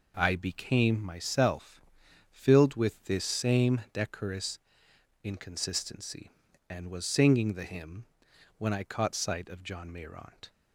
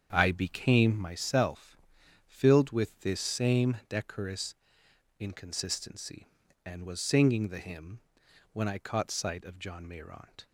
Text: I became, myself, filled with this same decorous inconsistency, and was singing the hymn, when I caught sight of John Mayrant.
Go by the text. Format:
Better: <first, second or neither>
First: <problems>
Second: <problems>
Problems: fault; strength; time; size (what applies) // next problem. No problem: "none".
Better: first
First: pauses between "decorous" and "inconsistency"; noticeable; at 4.5 s; 0.64 s long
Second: starts louder than the rest; strong; until 1.3 s; 7.5 dB // pauses between "decorous" and "inconsistency"; noticeable; at 4.5 s; 0.64 s long